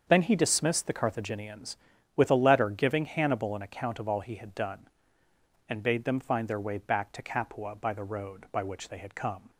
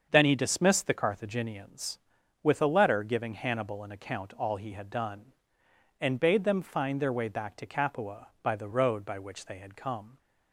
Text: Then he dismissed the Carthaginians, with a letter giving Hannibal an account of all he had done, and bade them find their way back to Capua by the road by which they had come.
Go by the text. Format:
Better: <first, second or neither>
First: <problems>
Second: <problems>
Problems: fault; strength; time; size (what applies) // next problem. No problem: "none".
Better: first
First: starts louder than the rest; until 1.0 s; 7 dB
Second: starts louder than the rest; until 1.1 s; 7 dB // skips "of"; at 4.3 s